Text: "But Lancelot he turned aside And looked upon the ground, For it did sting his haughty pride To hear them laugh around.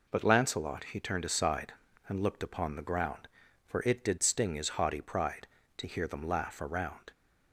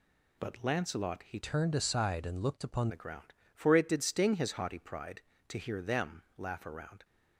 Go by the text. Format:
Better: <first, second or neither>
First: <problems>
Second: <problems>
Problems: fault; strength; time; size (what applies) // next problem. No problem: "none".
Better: first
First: none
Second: changes voice from "turned" to "upon"; from 1.4 to 2.8 s; 1.4 s long // pauses between "them" and "laugh"; slight; at 6.2 s; 0.16 s long